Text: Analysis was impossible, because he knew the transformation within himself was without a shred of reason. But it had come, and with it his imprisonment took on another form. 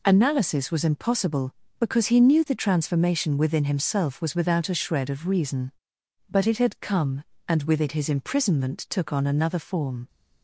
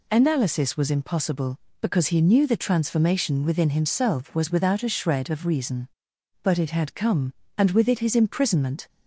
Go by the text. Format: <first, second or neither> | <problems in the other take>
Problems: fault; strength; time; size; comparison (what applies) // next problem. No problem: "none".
first | stops before "took on another form"; at 8.8 s